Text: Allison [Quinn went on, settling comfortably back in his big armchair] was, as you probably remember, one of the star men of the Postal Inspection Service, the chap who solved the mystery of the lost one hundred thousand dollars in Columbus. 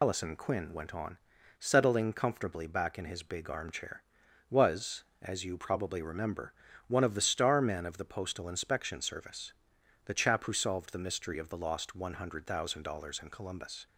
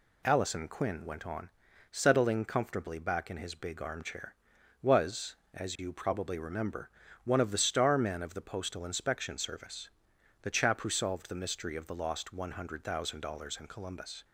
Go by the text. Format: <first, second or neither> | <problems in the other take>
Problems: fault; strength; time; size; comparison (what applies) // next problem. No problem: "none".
second | loses the start of "Allison"; at 0.0 s; 85 ms